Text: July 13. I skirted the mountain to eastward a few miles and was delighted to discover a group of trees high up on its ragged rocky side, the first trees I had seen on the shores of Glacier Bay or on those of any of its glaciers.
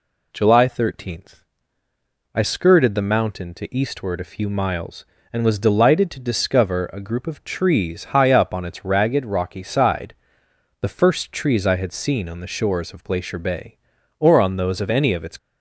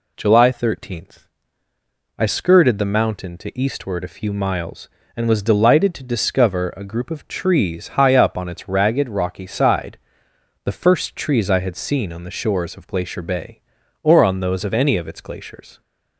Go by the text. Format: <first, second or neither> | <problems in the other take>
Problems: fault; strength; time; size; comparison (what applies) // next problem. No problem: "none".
second | stops before "glaciers"; at 15.3 s